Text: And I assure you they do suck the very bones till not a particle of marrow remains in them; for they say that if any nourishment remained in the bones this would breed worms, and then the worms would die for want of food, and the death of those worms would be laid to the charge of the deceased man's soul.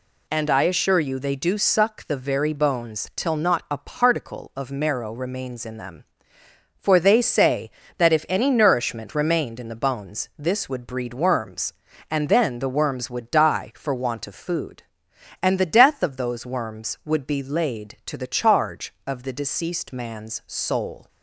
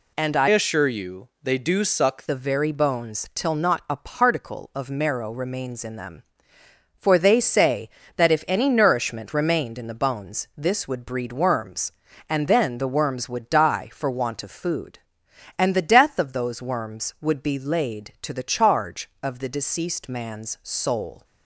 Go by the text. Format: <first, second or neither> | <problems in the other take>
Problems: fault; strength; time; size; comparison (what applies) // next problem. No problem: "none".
first | changes voice from "assure" to "suck"; from 0.4 to 2.2 s; 1.8 s long